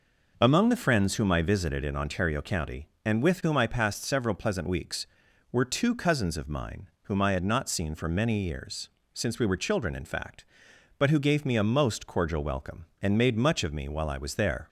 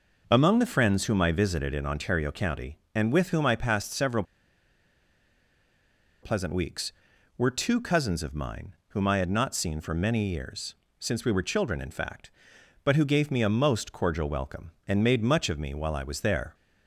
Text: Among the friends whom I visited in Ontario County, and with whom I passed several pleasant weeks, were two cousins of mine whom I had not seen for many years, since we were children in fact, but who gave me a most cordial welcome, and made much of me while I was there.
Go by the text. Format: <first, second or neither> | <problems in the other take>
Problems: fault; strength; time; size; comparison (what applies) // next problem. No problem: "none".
first | pauses between "several" and "pleasant"; strong; at 4.2 s; 1.9 s long